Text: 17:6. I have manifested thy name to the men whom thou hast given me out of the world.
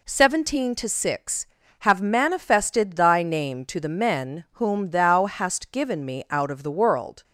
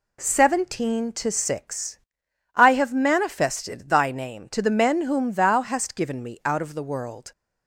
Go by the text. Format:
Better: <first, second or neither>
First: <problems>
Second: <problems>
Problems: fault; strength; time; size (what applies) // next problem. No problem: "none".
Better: second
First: skips "I"; at 1.6 s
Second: none